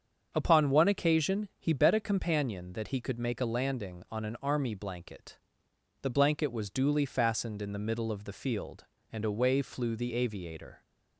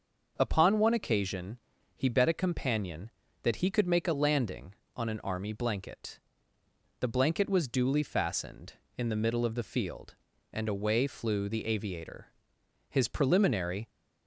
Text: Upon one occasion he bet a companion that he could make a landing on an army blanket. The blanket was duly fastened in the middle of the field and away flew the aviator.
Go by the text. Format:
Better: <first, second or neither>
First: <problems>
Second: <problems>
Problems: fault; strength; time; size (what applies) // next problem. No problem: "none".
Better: first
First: starts louder than the rest; strong; until 1.3 s; 7 dB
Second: starts louder than the rest; until 1.3 s; 6.5 dB // pauses between "occasion" and "he"; at 1.5 s; 0.38 s long // goes on to say "His preliminary"; noticeable; from 12.8 s on; 1.0 s long